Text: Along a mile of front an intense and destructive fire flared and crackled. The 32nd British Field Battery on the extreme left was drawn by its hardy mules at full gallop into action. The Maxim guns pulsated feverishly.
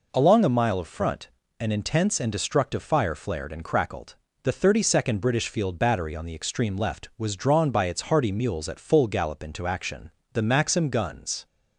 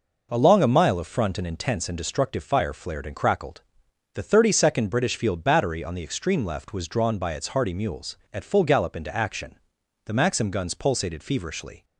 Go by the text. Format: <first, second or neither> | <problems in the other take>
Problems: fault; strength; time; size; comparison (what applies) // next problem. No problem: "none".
second | pauses between "front" and "an"; slight; at 1.2 s; 0.32 s long // stops before "pulsated feverishly"; at 11.4 s